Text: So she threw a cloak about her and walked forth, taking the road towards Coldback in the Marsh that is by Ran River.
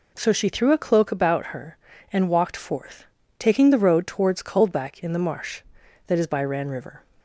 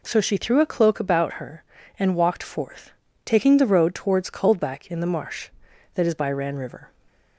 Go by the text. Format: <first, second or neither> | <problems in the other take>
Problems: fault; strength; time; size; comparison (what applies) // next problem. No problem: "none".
neither | none